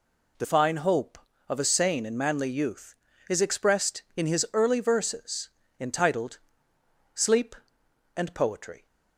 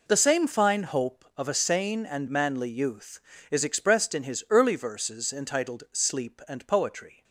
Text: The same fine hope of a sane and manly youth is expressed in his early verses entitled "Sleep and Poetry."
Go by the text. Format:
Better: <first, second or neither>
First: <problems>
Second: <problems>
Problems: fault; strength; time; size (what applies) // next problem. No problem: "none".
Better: second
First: skips "same"; at 0.4 s // pauses between "verses" and "entitled"; slight; at 5.4 s; 0.30 s long // pauses between "entitled" and "Sleep"; noticeable; at 6.3 s; 0.74 s long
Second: none